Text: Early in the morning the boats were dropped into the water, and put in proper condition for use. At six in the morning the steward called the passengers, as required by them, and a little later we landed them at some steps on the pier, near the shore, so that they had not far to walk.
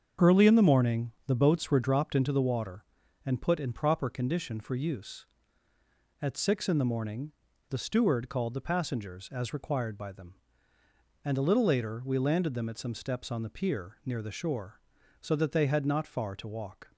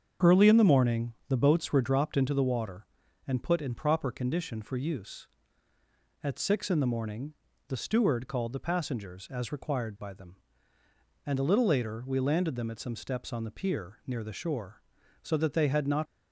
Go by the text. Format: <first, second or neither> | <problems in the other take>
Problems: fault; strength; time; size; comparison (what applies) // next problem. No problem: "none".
first | starts louder than the rest; strong; until 1.4 s; 7 dB; strong in the first // pauses between "morning" and "the"; slight; at 1.1 s; 0.16 s long; slight in the first // pauses between "morning" and "the"; slight; at 7.3 s; 0.36 s long; also in the first // stops before "far to walk"; at 16.0 s